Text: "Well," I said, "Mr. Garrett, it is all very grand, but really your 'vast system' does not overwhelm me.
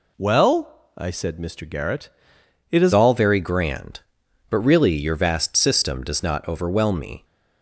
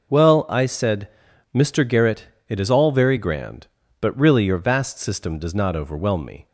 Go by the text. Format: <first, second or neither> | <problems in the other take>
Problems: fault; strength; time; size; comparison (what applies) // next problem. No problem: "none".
second | changes voice at "all"; from 2.9 s on; 4.3 s long